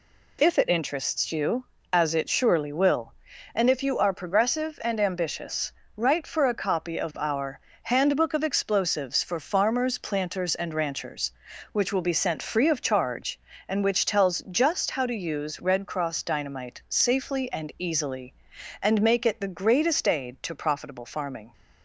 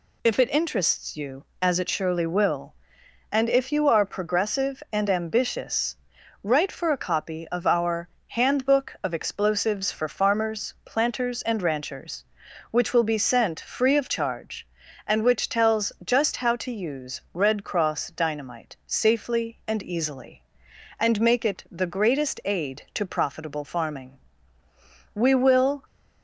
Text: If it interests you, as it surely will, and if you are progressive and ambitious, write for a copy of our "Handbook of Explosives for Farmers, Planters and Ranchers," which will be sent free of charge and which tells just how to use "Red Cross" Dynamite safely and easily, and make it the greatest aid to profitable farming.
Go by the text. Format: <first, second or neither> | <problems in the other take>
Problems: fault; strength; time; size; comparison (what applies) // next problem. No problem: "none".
first | pauses between "our" and "Handbook"; slight; at 8.0 s; 0.18 s long; slight in the first // goes on to say "We will"; noticeable; from 25.1 s on; 0.70 s long